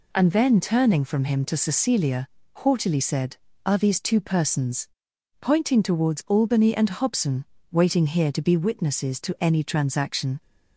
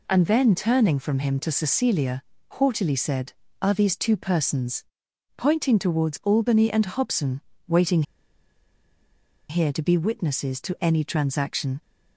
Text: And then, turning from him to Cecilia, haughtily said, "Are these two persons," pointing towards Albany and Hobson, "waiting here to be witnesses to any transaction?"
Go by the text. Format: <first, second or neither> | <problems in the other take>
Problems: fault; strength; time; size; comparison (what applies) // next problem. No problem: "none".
first | pauses between "waiting" and "here"; strong; at 8.0 s; 1.4 s long